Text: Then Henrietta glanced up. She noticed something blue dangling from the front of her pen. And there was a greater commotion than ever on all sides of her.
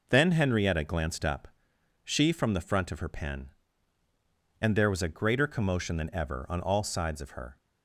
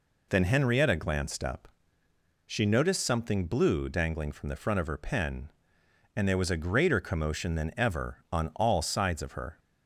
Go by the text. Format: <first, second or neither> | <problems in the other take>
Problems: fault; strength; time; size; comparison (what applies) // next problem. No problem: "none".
second | skips "noticed something blue dangling"; at 2.3 s